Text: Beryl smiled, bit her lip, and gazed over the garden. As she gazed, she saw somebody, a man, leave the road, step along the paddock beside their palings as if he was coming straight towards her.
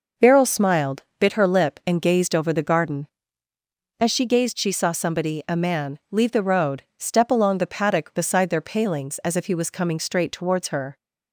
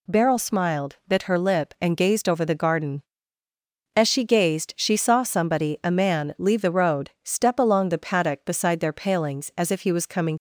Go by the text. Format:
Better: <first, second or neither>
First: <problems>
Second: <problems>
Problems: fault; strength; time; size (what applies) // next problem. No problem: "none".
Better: first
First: none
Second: stops before "straight towards her"; at 10.3 s